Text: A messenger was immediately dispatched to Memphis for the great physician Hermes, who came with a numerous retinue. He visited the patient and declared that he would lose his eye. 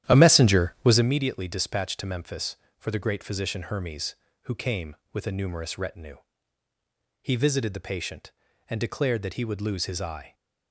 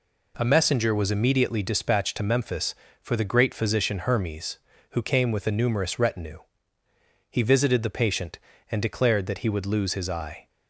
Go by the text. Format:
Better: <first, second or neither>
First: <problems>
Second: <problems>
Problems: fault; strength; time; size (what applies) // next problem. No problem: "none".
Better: second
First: starts louder than the rest; strong; until 1.2 s; 11.5 dB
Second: none